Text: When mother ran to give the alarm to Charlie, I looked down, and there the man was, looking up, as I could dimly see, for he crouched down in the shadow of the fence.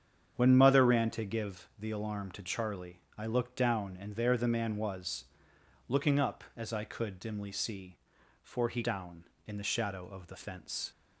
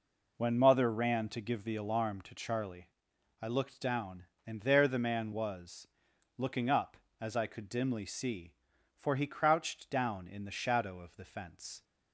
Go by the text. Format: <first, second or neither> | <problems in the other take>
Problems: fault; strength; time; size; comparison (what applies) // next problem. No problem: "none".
second | starts louder than the rest; strong; until 1.3 s; 8 dB // skips "crouched"; at 8.8 s